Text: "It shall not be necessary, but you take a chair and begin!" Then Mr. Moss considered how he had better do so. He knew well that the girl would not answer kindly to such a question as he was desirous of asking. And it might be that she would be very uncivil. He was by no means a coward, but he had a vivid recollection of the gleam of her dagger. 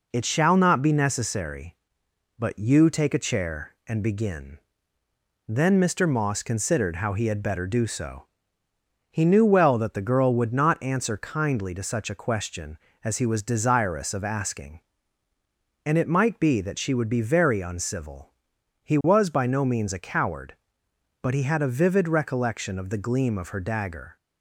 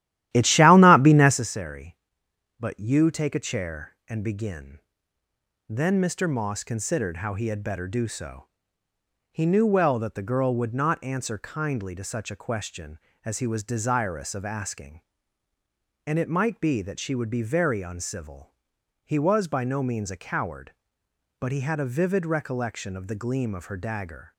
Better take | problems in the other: first | starts louder than the rest; strong; until 1.4 s; 13.5 dB

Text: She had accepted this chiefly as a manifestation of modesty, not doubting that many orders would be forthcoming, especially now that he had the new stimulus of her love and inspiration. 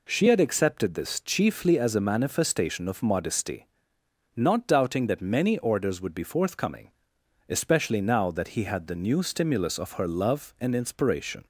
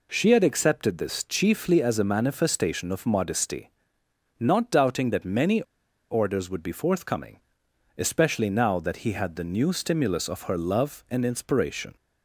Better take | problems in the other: first | pauses between "many" and "orders"; noticeable; at 5.6 s; 0.48 s long

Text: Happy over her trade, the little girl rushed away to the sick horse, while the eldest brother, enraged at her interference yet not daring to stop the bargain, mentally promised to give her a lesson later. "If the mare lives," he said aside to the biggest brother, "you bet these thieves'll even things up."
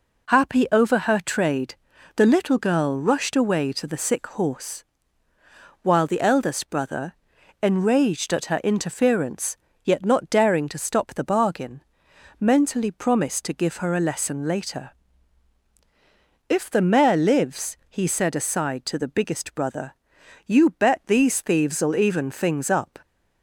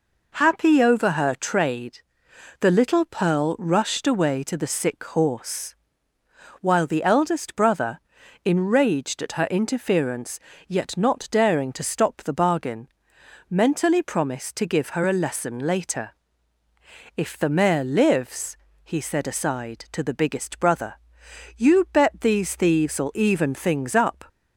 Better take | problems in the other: first | says "pearl" for "girl"; at 3.0 s // pauses between "interference" and "yet"; slight; at 10.3 s; 0.28 s long; slight in the first

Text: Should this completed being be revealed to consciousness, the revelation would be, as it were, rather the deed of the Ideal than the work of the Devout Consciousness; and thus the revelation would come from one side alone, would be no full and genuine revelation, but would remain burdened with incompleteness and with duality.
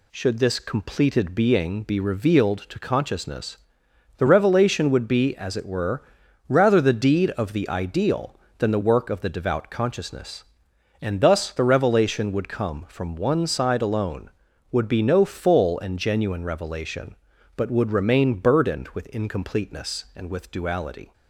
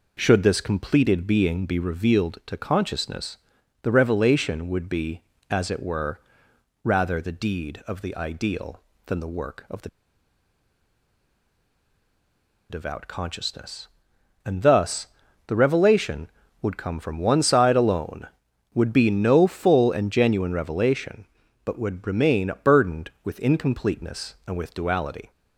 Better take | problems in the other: first | pauses between "the" and "Devout"; strong; at 9.8 s; 2.8 s long // pauses between "thus" and "the"; at 15.0 s; 0.40 s long

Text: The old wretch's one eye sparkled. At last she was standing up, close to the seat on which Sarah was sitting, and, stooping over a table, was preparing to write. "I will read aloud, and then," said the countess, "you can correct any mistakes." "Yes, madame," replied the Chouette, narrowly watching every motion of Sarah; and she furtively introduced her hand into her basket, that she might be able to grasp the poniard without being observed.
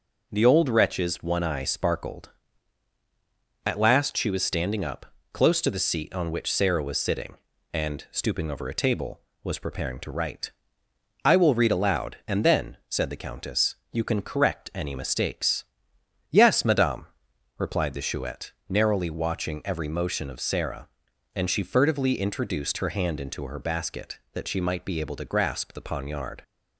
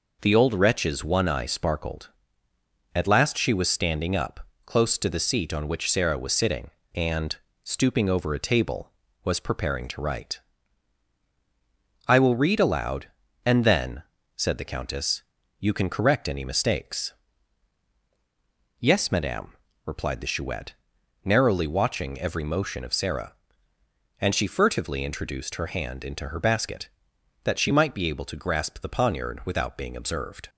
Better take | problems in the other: second | stops before "without being observed"; at 26.4 s

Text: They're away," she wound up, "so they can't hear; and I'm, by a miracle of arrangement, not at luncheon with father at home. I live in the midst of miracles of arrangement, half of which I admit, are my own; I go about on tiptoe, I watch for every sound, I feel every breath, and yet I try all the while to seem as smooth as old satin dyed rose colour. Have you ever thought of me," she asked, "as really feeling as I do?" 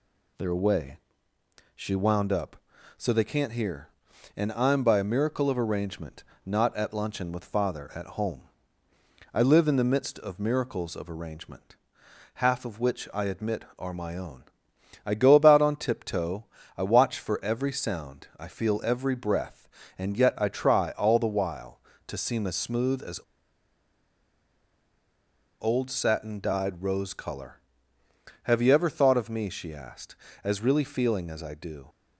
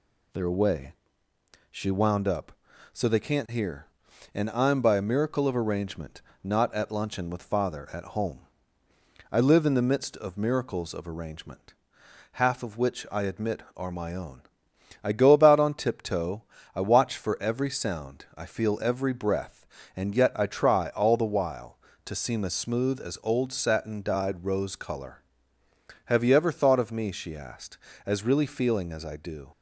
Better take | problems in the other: second | pauses between "as" and "old"; strong; at 23.2 s; 2.3 s long

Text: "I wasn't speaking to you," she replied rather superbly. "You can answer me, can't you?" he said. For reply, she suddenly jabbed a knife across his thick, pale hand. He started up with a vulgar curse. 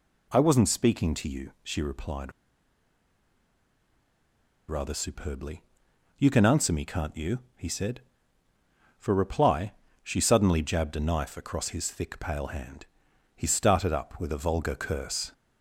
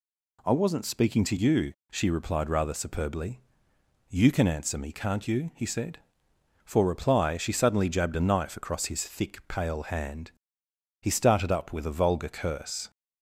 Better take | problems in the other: second | pauses between "replied" and "rather"; strong; at 2.3 s; 2.3 s long

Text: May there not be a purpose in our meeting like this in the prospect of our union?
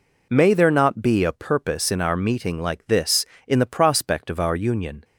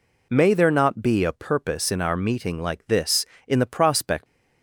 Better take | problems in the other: first | stops before "of our union"; at 4.2 s

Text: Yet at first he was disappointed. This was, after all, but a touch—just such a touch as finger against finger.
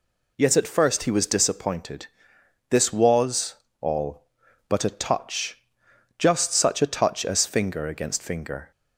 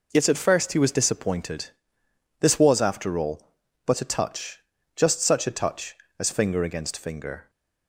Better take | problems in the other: second | skips "after"; at 3.6 s

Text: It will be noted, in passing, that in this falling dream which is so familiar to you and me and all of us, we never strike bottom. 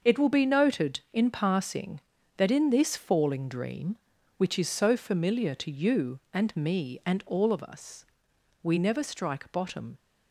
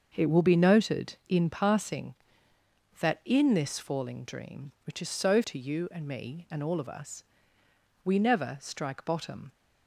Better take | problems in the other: first | starts louder than the rest; until 1.1 s; 6 dB; also in the first // skips "familiar"; at 5.4 s

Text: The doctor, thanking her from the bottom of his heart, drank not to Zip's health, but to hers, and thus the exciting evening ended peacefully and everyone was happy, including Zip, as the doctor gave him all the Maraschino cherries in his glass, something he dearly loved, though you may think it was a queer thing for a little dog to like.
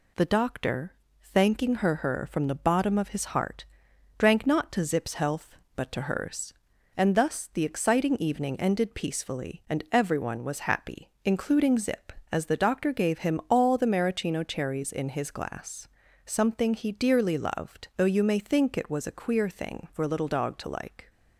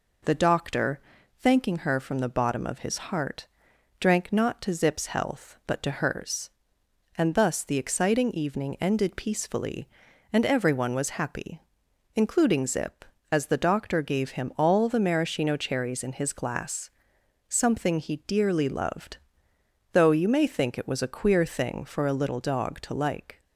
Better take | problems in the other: second | says "her" twice; at 1.9 s

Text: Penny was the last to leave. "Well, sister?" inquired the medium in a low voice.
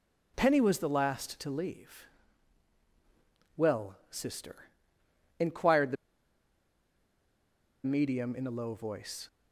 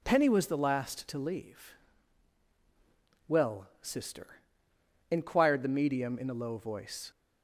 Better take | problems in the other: second | pauses between "the" and "medium"; strong; at 5.9 s; 1.8 s long

